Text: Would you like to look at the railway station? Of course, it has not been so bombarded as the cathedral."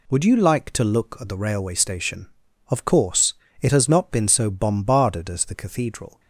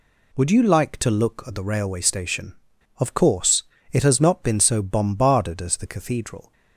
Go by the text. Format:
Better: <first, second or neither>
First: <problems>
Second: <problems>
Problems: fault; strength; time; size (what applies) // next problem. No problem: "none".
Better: neither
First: none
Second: none